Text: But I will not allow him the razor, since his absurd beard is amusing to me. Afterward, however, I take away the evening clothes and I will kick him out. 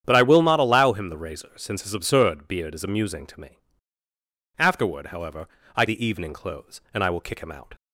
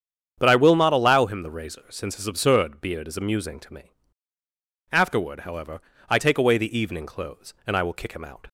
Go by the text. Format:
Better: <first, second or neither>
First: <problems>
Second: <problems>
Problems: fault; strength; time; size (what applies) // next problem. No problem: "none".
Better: second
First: starts louder than the rest; strong; until 1.0 s; 9 dB // skips "take away"; at 5.8 s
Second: starts louder than the rest; strong; until 1.3 s; 8 dB